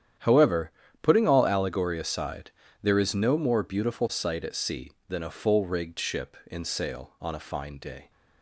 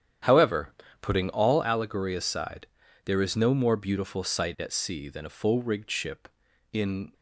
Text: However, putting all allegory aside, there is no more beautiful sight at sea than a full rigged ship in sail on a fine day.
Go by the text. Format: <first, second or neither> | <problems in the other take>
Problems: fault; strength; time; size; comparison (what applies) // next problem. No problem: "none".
first | starts louder than the rest; strong; until 1.5 s; 9.5 dB; strong in the first // stops before "sail on a fine day"; at 7.1 s